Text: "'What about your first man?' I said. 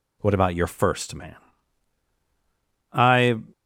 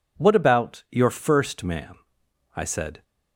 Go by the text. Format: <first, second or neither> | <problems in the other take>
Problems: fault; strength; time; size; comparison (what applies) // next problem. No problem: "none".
second | stops before "said"; at 3.5 s